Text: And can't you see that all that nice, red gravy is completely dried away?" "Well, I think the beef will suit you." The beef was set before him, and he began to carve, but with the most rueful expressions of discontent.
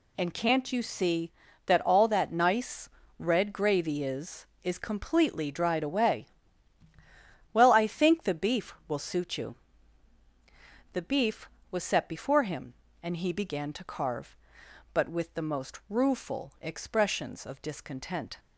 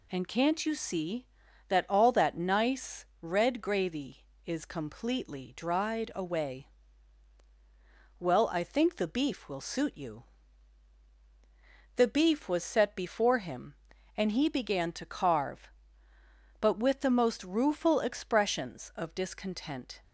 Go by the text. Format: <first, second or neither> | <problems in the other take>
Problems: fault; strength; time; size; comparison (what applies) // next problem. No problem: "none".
second | says "is" twice; at 4.6 s